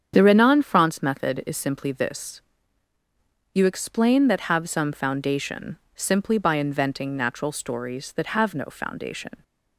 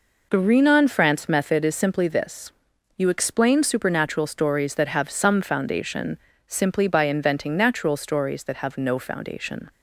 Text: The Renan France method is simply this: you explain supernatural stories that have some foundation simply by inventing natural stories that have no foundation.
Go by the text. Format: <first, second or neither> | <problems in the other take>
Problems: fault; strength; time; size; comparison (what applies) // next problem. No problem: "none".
second | starts louder than the rest; strong; until 1.1 s; 8 dB // skips "supernatural stories"; at 4.2 s // pauses between "foundation" and "simply"; slight; at 5.7 s; 0.20 s long; slight in the second